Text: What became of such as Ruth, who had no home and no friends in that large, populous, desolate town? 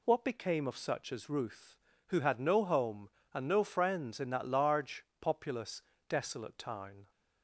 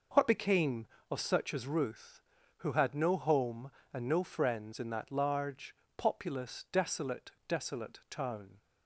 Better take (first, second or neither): first